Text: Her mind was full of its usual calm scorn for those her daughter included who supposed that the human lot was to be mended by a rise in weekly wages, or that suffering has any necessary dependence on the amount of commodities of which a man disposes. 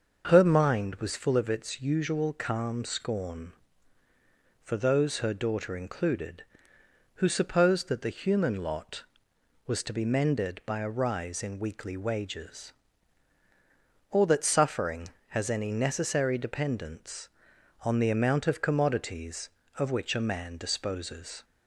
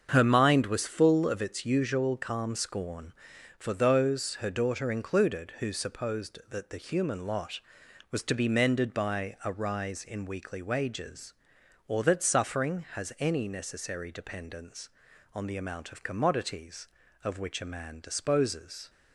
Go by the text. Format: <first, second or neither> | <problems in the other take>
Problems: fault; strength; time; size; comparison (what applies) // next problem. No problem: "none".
neither | starts louder than the rest; the same in both